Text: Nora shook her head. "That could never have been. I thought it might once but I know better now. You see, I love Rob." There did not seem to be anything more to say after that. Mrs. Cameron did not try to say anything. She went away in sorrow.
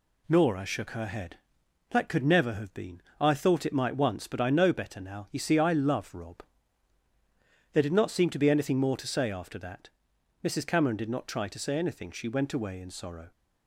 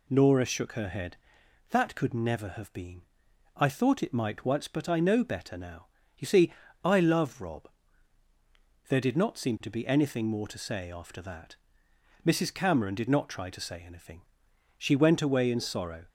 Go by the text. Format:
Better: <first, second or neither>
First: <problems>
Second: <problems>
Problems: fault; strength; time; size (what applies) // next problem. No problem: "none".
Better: neither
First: none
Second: none